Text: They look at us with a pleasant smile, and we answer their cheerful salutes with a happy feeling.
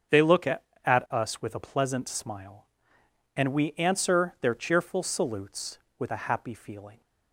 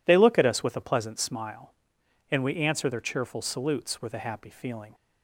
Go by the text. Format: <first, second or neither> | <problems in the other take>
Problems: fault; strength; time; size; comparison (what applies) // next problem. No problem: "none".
second | starts louder than the rest; until 1.4 s; 7 dB // says "at" twice; at 0.8 s